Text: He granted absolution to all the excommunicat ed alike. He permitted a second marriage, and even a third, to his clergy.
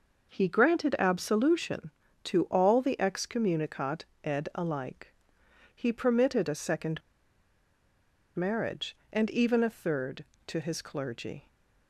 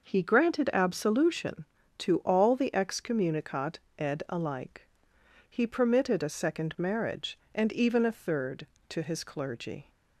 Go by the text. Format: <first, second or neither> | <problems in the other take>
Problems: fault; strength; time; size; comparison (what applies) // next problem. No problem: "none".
second | pauses between "excommunicat" and "ed"; slight; at 4.0 s; 0.20 s long; slight in the second // pauses between "second" and "marriage"; strong; at 7.0 s; 1.3 s long